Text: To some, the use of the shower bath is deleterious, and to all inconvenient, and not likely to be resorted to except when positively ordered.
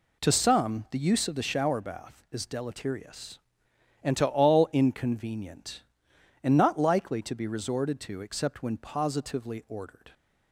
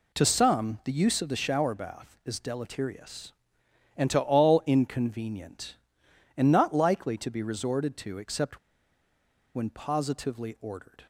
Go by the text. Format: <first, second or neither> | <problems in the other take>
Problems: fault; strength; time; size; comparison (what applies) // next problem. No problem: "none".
first | pauses between "except" and "when"; noticeable; at 8.5 s; 0.97 s long